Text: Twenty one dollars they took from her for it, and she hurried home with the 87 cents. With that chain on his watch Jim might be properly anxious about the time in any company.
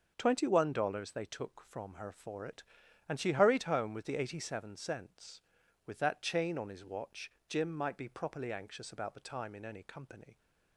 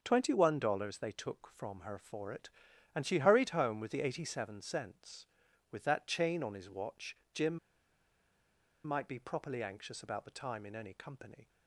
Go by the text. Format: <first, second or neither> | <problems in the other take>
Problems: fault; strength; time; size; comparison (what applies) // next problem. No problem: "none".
first | starts louder than the rest; until 1.0 s; 6.5 dB; also in the first // pauses between "watch" and "Jim"; slight; at 7.1 s; 0.20 s long; slight in the first // pauses between "Jim" and "might"; strong; at 7.5 s; 1.2 s long